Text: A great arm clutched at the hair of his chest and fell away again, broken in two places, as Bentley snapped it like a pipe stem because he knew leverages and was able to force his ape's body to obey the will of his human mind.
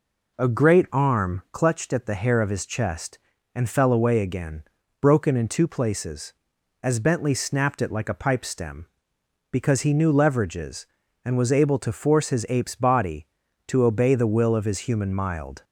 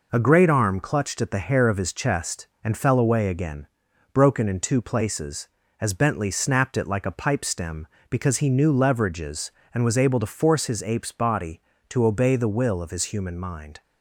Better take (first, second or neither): second